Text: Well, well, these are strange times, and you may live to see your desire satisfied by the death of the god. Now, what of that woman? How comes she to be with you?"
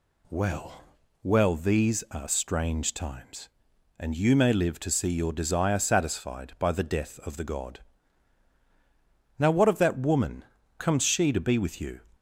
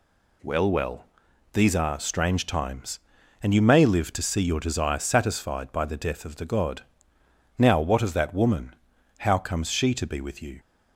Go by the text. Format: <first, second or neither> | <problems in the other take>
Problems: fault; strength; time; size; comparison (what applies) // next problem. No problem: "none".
second | skips "How"; at 10.6 s